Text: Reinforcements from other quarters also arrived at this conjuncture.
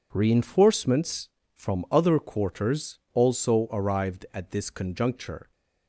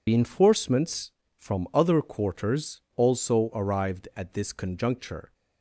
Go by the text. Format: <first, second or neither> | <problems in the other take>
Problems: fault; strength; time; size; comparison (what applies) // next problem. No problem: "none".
first | loses the start of "Reinforcements"; at 0.0 s; 135 ms